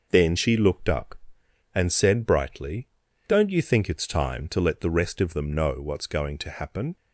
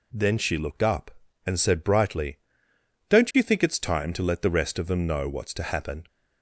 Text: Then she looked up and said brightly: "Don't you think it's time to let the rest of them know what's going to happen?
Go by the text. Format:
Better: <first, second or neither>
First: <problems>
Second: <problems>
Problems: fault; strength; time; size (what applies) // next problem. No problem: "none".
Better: first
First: none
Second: skips "going"; at 5.5 s